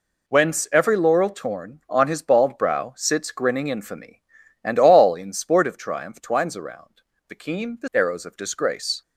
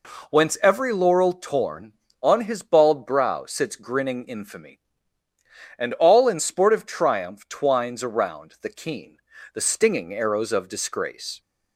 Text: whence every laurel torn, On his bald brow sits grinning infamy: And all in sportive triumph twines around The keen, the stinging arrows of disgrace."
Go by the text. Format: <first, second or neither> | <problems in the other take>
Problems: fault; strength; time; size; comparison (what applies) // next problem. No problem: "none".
second | pauses between "around" and "The"; slight; at 7.0 s; 0.26 s long // skips "stinging"; at 7.9 s